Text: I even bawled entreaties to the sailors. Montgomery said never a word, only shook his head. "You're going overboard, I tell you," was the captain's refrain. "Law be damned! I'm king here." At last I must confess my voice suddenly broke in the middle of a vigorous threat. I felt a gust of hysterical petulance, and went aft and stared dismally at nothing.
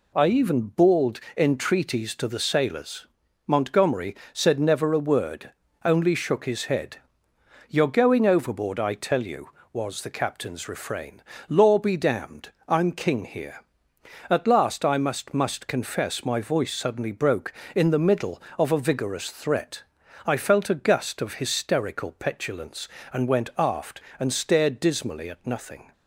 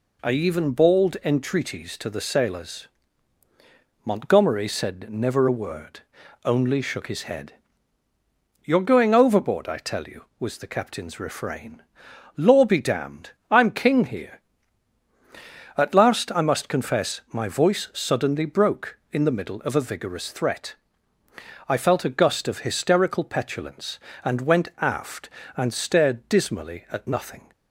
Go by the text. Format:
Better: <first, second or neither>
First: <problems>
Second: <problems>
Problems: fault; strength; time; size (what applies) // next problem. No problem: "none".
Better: second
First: pauses between "bawled" and "entreaties"; slight; at 1.1 s; 0.16 s long // pauses between "Montgomery" and "said"; slight; at 4.1 s; 0.18 s long // says "must" twice; at 15.3 s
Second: none